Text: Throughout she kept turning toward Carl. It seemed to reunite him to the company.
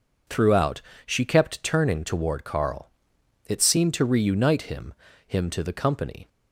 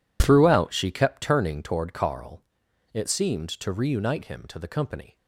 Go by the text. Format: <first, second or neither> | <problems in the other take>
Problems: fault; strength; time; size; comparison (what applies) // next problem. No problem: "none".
second | pauses between "Throughout" and "she"; slight; at 0.8 s; 0.24 s long // says "him" twice; at 5.2 s